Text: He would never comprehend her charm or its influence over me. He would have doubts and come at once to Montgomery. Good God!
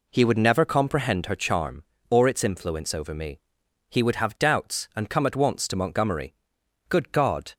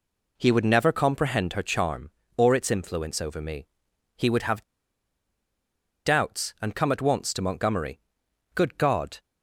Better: first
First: none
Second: pauses between "have" and "doubts"; strong; at 4.6 s; 1.4 s long

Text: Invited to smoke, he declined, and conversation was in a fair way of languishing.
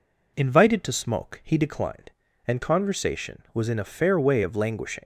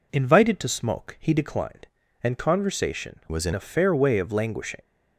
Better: first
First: none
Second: changes voice from "was" to "in"; from 3.3 to 3.5 s; 0.2 s long

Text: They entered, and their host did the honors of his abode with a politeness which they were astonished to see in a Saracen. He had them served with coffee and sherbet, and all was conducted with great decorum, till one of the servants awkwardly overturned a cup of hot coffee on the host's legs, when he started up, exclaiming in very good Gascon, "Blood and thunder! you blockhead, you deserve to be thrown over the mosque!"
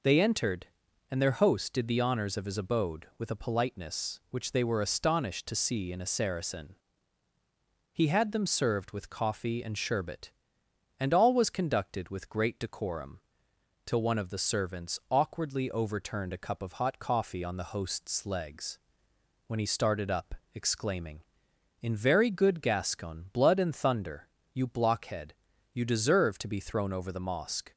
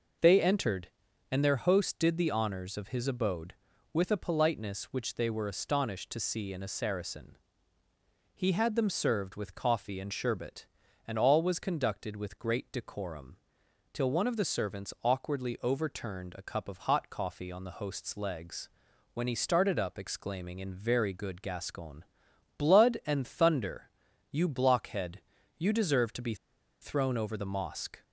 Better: first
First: none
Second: pauses between "be" and "thrown"; noticeable; at 26.3 s; 0.46 s long

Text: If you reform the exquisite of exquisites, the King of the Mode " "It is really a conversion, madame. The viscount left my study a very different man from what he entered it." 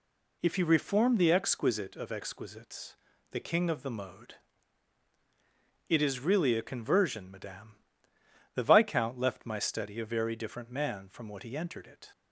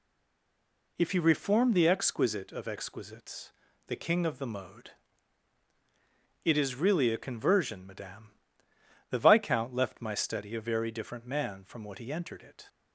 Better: first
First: none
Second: stays silent before the first word; until 0.9 s; 0.9 s long

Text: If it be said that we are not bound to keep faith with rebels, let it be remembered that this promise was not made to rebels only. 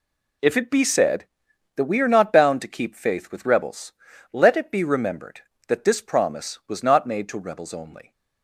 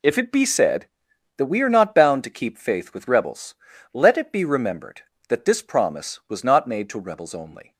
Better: neither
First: none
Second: none

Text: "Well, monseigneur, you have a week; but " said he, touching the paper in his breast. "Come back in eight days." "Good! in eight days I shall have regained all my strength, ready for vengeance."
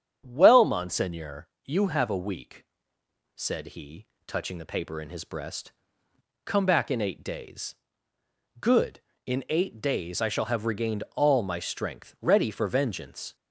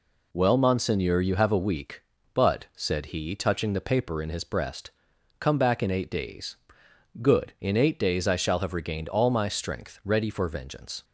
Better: second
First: starts louder than the rest; strong; until 1.2 s; 9 dB // skips "but"; at 2.8 s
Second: none

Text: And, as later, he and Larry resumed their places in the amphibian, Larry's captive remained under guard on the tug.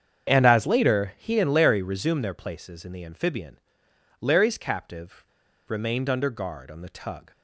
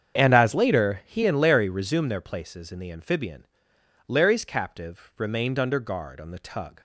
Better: second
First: starts louder than the rest; strong; until 1.3 s; 7.5 dB // pauses between "captive" and "remained"; at 5.2 s; 0.42 s long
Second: starts louder than the rest; strong; until 1.2 s; 7.5 dB

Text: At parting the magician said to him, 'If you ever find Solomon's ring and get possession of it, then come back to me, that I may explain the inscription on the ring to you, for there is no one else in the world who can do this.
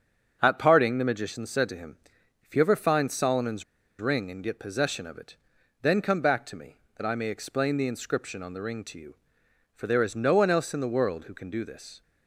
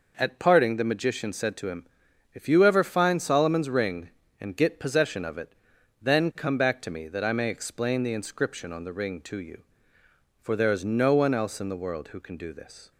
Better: second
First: starts louder than the rest; until 1.4 s; 6.5 dB // pauses between "Solomon's" and "ring"; at 3.6 s; 0.38 s long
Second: none

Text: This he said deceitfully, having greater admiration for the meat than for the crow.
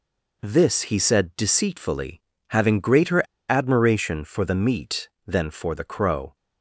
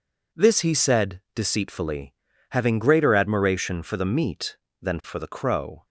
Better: second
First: pauses between "greater" and "admiration"; slight; at 3.2 s; 0.28 s long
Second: none

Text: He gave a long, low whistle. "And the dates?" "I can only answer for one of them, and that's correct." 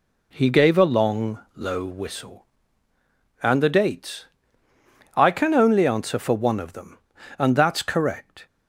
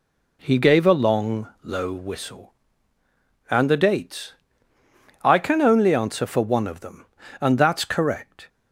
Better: neither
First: none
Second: none

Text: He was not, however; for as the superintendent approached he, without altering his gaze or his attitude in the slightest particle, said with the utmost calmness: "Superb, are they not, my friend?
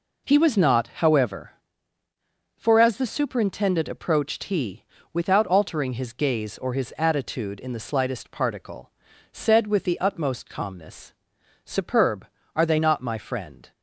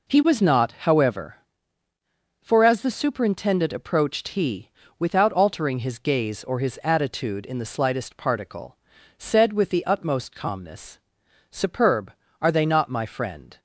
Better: neither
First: none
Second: none

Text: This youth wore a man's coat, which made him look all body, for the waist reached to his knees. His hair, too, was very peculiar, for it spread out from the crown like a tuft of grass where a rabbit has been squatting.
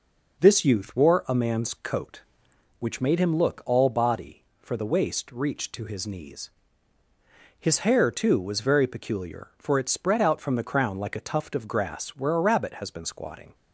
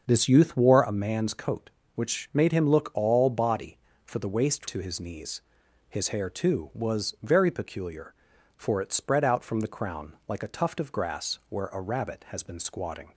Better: first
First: none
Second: starts louder than the rest; until 1.0 s; 6.5 dB // skips "reached"; at 4.6 s

